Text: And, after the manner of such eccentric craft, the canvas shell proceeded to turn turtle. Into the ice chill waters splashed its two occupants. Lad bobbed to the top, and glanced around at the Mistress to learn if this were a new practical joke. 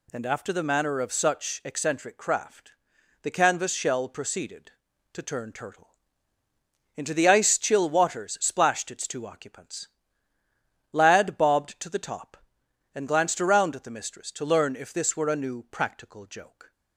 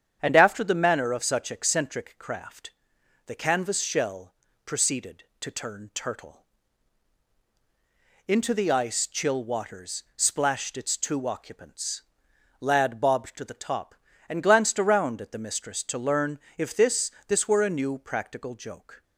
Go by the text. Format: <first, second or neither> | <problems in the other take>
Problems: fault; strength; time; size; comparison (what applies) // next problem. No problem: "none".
first | starts louder than the rest; strong; until 1.2 s; 8.5 dB // pauses between "shell" and "proceeded"; slight; at 4.3 s; 0.30 s long // pauses between "learn" and "if"; slight; at 16.3 s; 0.18 s long // says "this" twice; at 17.2 s